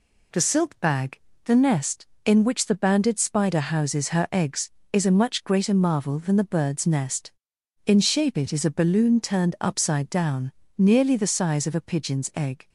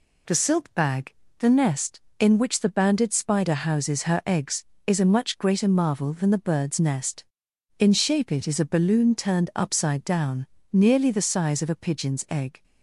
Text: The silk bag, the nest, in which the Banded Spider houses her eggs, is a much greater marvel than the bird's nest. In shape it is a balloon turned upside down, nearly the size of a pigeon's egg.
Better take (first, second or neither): neither